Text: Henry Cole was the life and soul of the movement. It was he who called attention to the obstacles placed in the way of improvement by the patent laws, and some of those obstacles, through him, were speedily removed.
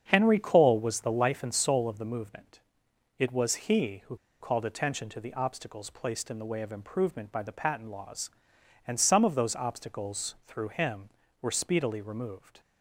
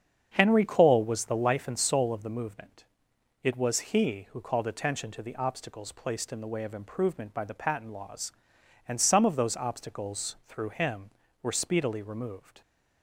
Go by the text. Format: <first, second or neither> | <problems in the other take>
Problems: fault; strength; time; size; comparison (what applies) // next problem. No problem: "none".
second | starts louder than the rest; strong; until 1.1 s; 7.5 dB; strong in the second // pauses between "who" and "called"; slight; at 4.1 s; 0.24 s long